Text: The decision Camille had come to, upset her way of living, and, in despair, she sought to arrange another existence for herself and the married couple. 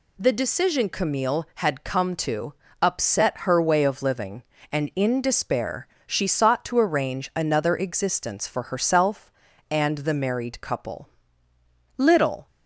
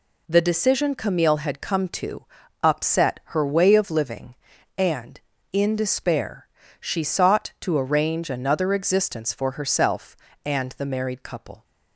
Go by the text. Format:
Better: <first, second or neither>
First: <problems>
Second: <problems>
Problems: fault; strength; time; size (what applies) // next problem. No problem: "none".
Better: second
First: goes on to say "Little"; slight; from 11.9 s on; 0.48 s long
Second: none